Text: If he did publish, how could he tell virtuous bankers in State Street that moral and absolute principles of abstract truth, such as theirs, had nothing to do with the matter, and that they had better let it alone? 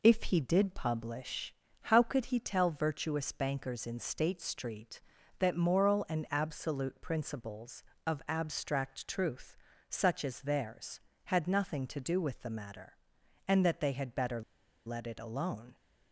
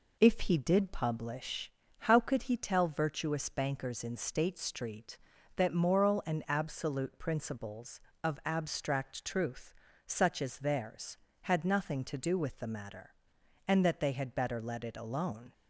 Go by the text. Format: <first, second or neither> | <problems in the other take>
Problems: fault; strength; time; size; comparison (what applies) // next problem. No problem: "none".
second | pauses between "better" and "let"; at 14.4 s; 0.45 s long